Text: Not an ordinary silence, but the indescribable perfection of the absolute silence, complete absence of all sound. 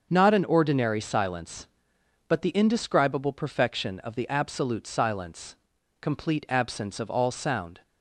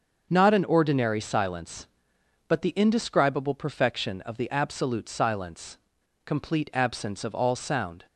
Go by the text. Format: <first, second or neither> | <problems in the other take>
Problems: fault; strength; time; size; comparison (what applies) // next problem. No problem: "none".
neither | starts louder than the rest; the same in both